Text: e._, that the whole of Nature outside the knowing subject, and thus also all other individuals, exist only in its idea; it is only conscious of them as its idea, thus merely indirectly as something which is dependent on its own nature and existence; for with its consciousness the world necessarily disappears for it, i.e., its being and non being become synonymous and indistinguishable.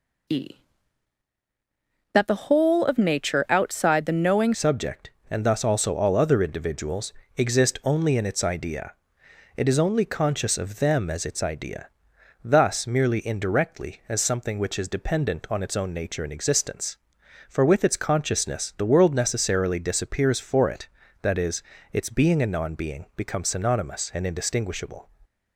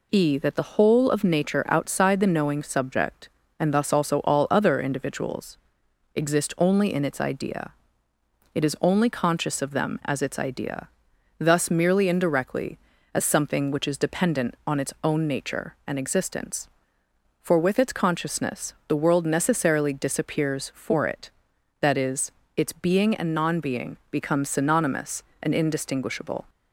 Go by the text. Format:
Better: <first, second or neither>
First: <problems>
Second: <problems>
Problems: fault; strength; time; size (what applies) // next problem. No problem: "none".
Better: second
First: changes voice at "subject"; from 4.5 s on; 20.5 s long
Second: none